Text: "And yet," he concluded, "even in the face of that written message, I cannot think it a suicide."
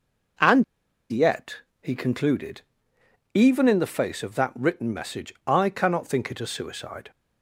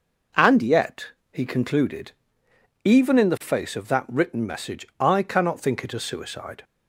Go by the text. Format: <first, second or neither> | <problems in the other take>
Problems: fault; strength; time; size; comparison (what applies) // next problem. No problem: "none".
second | pauses between "And" and "yet"; noticeable; at 0.6 s; 0.48 s long